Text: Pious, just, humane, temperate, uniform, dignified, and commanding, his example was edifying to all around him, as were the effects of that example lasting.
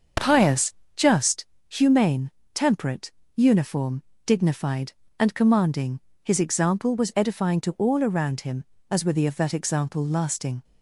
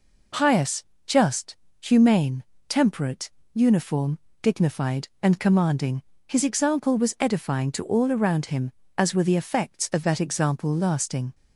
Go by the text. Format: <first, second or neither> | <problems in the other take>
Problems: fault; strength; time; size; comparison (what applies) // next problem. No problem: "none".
second | starts louder than the rest; until 1.4 s; 6.5 dB // skips "effects"; at 9.2 s